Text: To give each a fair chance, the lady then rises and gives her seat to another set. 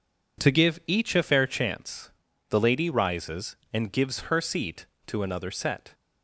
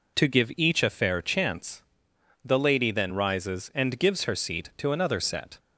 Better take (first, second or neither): second